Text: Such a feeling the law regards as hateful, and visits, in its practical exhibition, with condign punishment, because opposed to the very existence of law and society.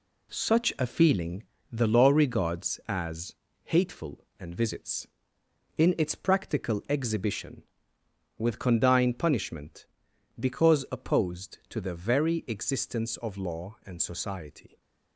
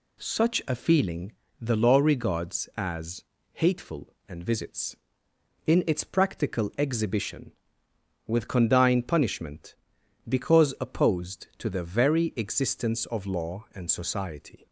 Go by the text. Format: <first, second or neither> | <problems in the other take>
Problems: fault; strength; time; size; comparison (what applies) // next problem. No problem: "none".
second | gets quieter; throughout; 7 dB // pauses between "feeling" and "the"; slight; at 1.4 s; 0.30 s long; slight in the second // pauses between "as" and "hateful"; slight; at 3.3 s; 0.30 s long; slight in the second